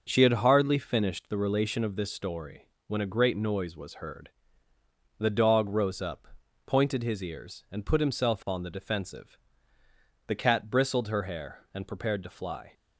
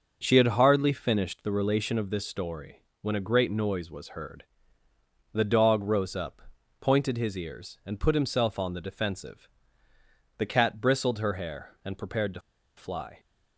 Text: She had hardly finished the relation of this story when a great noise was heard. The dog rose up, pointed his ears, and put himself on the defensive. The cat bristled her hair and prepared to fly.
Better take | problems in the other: first | pauses between "story" and "when"; slight; at 2.8 s; 0.16 s long; slight in the first // pauses between "to" and "fly"; at 12.3 s; 0.36 s long

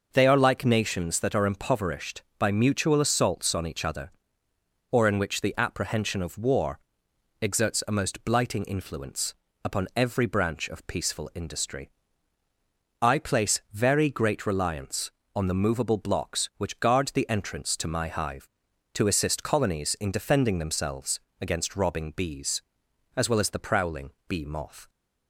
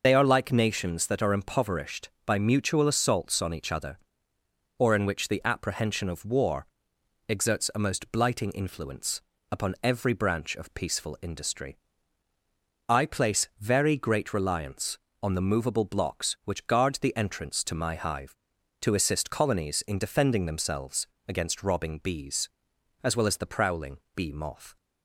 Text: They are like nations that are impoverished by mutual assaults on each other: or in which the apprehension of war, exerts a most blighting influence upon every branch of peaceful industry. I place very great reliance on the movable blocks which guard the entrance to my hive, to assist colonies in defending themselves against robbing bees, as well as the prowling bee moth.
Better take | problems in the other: first | loses the start of "They"; at 0.0 s; 50 ms // pauses between "influence" and "upon"; slight; at 9.2 s; 0.28 s long; slight in the first // pauses between "themselves" and "against"; slight; at 21.0 s; 0.20 s long; slight in the first // pauses between "prowling" and "bee"; slight; at 23.9 s; 0.16 s long; slight in the first

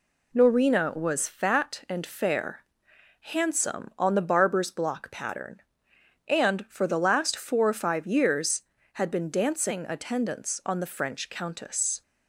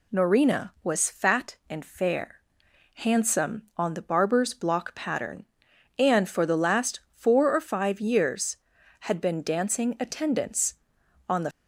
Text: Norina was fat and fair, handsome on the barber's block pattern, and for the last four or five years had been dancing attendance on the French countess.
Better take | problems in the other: first | stops before "French countess"; at 11.5 s

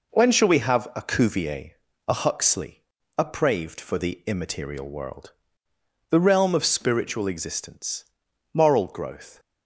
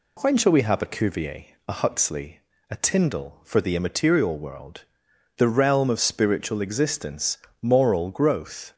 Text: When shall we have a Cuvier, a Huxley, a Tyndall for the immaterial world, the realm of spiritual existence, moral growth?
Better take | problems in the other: second | says "Praved" for "Tyndall"; at 3.2 s

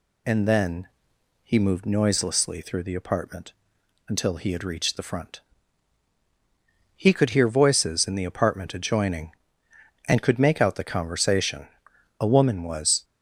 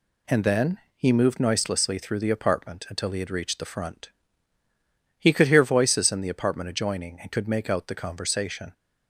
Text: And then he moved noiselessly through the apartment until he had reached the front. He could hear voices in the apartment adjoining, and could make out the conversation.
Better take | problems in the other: second | pauses between "then" and "he"; noticeable; at 0.8 s; 0.54 s long; slight in the second // pauses between "apartment" and "until"; noticeable; at 3.5 s; 0.56 s long // goes on to say "A woman was"; noticeable; from 12.2 s on; 0.84 s long

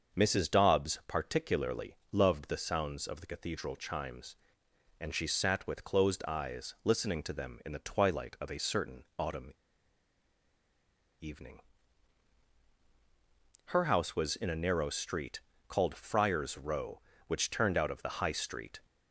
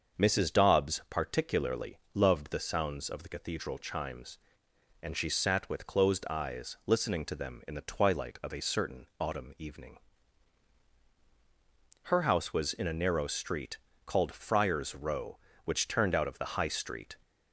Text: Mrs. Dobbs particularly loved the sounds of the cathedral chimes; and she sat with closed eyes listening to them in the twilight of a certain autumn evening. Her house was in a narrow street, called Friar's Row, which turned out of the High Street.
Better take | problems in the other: second | starts louder than the rest; until 1.2 s; 6.5 dB; also in the second // pauses between "particularly" and "loved"; slight; at 1.9 s; 0.16 s long; slight in the second // pauses between "autumn" and "evening"; strong; at 9.5 s; 1.6 s long

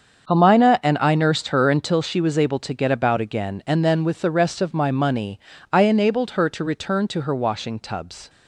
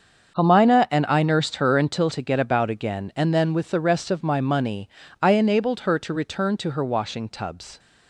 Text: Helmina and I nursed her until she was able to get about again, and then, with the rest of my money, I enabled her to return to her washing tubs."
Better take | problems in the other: first | starts louder than the rest; until 1.4 s; 7 dB; also in the first // skips "she was able"; at 2.0 s

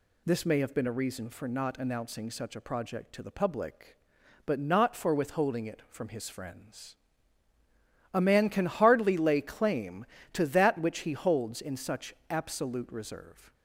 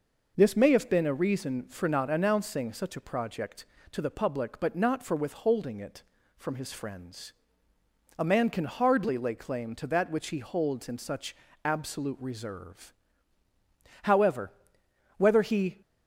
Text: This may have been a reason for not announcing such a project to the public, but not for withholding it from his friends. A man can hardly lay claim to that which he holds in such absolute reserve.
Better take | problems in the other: first | pauses between "such" and "absolute"; slight; at 11.3 s; 0.28 s long; slight in the first // goes on to say "However whether he"; strong; from 14.0 s on; 1.7 s long

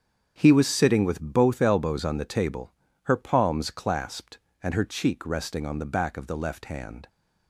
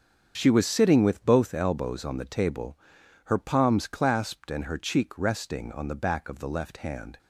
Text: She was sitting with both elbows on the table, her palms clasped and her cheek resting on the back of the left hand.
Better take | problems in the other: second | starts louder than the rest; strong; until 1.3 s; 7.5 dB; strong in the second // says "He" for "She"; at 0.3 s

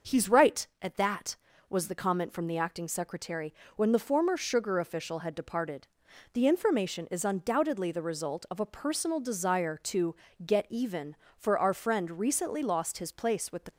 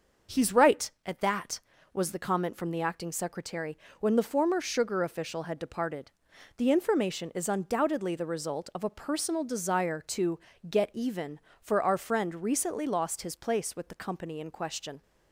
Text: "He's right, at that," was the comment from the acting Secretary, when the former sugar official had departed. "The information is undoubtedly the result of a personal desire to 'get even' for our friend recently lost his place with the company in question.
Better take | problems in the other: second | starts louder than the rest; until 1.2 s; 6.5 dB; also in the second // pauses between "to" and "get"; slight; at 10.1 s; 0.32 s long; slight in the second // stops before "company in question"; at 13.7 s

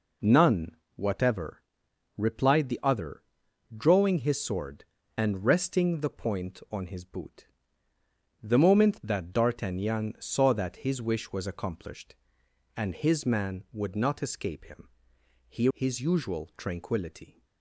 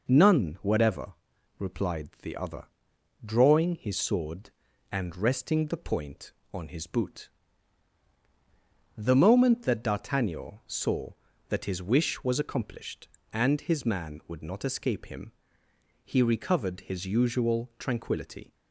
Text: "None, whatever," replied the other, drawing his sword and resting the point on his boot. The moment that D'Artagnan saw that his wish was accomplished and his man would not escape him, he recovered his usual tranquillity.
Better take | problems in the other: second | skips "recovered"; at 15.6 s

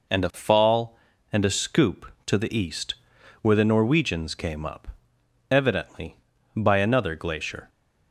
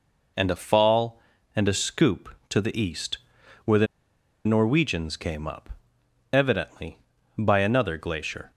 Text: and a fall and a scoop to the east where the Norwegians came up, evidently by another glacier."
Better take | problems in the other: first | pauses between "east" and "where"; noticeable; at 3.1 s; 0.46 s long; noticeable in the first // pauses between "the" and "Norwegians"; noticeable; at 3.8 s; 0.60 s long

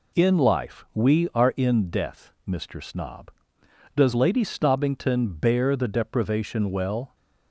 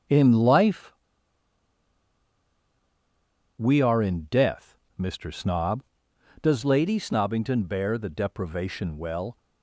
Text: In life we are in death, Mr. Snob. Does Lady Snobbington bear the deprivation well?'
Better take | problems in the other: first | starts louder than the rest; until 3.7 s; 7 dB // pauses between "life" and "we"; strong; at 0.9 s; 2.6 s long

